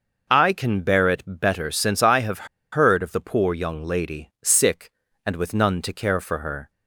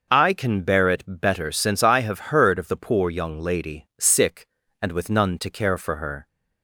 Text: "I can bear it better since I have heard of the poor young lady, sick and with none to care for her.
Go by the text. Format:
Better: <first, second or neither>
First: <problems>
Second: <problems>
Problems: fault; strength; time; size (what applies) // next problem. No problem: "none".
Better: second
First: pauses between "have" and "heard"; slight; at 2.4 s; 0.26 s long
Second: none